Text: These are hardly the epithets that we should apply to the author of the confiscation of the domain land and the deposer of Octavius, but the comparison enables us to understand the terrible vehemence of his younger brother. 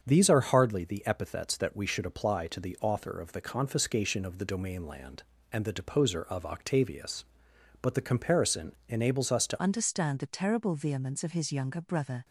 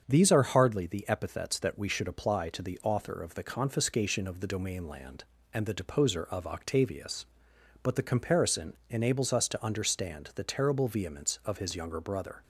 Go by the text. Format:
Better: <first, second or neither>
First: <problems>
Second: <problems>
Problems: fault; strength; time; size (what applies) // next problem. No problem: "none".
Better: second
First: starts louder than the rest; until 1.0 s; 7 dB // changes voice at "understand"; from 9.6 s on; 2.6 s long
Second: starts louder than the rest; until 1.0 s; 7 dB